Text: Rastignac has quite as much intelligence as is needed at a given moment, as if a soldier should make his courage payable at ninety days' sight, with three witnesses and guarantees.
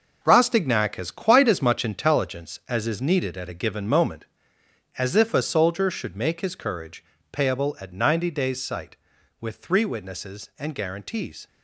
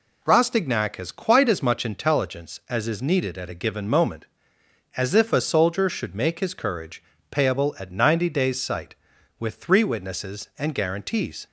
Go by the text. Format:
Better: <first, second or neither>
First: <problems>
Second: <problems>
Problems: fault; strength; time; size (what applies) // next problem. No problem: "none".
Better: second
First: gets quieter; strong; throughout; 9 dB // pauses between "courage" and "payable"; slight; at 7.0 s; 0.28 s long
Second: pauses between "courage" and "payable"; slight; at 7.0 s; 0.28 s long